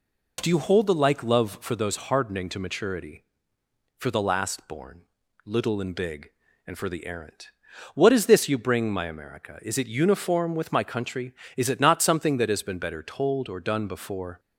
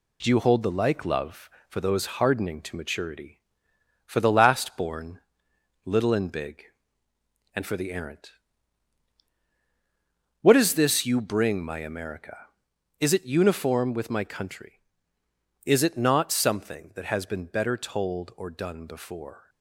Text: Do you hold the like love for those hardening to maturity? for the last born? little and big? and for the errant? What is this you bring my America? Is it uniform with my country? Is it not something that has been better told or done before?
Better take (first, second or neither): first